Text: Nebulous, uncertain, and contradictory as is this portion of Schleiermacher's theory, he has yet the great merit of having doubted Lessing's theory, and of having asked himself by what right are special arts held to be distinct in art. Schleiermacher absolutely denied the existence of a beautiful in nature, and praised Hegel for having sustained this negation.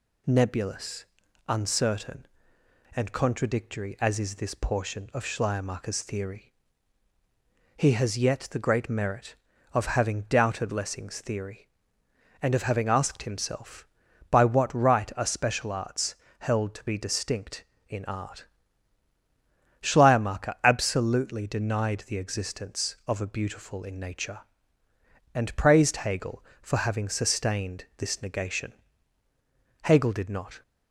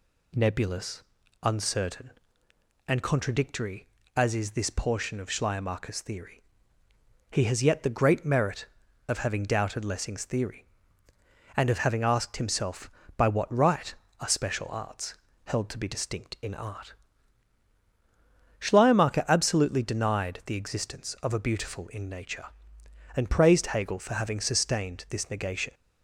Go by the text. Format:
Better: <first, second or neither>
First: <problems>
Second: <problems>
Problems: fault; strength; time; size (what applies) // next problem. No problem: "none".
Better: second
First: pauses between "arts" and "held"; slight; at 16.1 s; 0.24 s long // goes on to say "Hegel did not"; noticeable; from 29.8 s on; 0.78 s long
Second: pauses between "arts" and "held"; slight; at 15.1 s; 0.30 s long